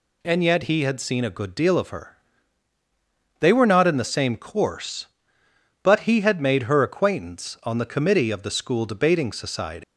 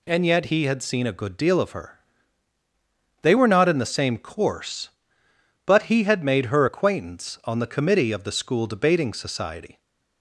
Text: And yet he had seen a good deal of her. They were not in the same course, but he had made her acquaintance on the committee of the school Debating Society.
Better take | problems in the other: second | leaves "Society" unfinished; at 9.8 s; 155 ms

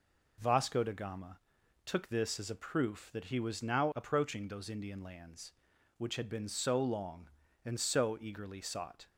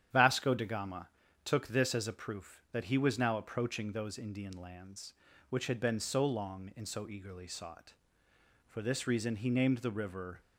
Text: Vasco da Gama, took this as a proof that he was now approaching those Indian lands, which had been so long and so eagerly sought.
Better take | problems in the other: first | starts louder than the rest; strong; until 1.4 s; 9.5 dB // goes on to say "For this reason he named the river"; strong; from 8.6 s on; 1.7 s long

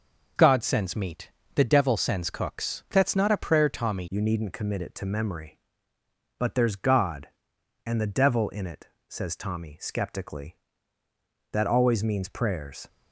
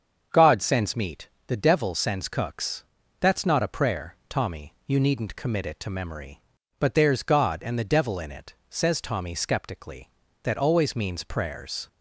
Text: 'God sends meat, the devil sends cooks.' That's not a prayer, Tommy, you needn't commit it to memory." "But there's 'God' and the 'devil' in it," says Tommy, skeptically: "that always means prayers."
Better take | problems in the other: second | starts louder than the rest; noticeable; until 1.6 s; 6 dB; also in the second // changes voice at "you"; from 4.0 s on; 8.8 s long

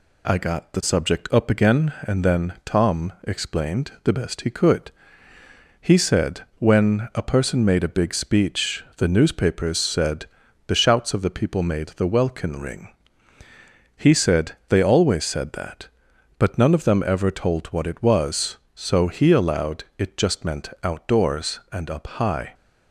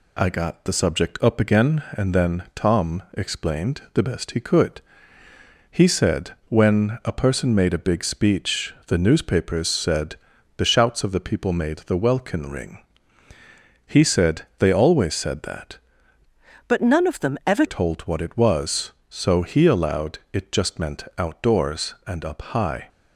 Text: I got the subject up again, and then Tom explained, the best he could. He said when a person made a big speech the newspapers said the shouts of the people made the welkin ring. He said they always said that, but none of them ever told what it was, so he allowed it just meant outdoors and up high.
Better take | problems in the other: first | pauses between "said" and "when"; slight; at 6.3 s; 0.16 s long; slight in the first // pauses between "said" and "the"; at 10.1 s; 0.40 s long; also in the first // pauses between "said" and "they"; slight; at 14.4 s; 0.16 s long; slight in the first // changes voice from "but" to "ever"; from 16.6 to 17.6 s; 1.0 s long

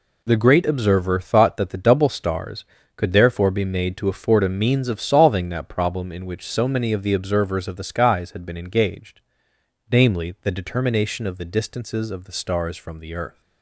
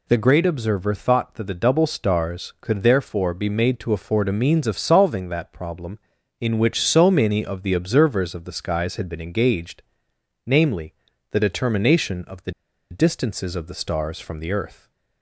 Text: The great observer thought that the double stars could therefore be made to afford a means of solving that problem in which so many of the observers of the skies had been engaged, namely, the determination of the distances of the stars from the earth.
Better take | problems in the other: first | pauses between "the" and "distances"; at 12.5 s; 0.38 s long

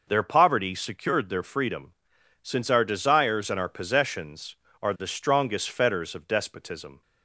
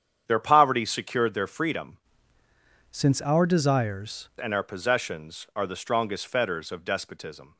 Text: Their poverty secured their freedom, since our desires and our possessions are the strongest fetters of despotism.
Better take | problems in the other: first | starts louder than the rest; strong; until 1.2 s; 8.5 dB // changes voice from "since" to "desires"; from 2.8 to 4.2 s; 1.4 s long

